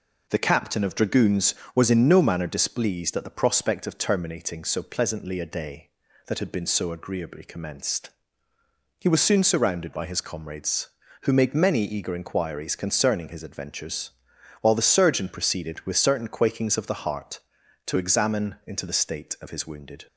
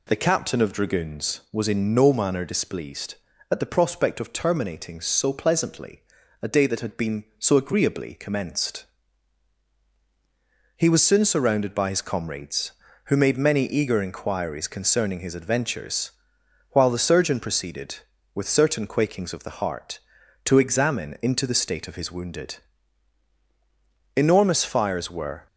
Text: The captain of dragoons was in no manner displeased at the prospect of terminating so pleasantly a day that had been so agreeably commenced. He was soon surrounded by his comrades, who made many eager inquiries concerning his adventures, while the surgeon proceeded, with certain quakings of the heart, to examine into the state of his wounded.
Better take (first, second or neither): first